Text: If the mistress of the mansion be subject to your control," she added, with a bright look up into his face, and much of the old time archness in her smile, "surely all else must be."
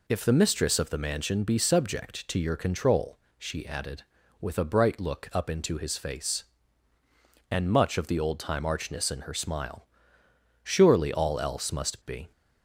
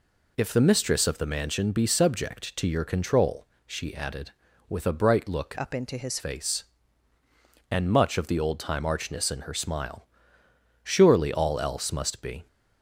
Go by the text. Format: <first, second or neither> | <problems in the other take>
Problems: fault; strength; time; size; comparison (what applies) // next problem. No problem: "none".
first | changes voice from "up" to "his"; from 5.5 to 6.1 s; 0.6 s long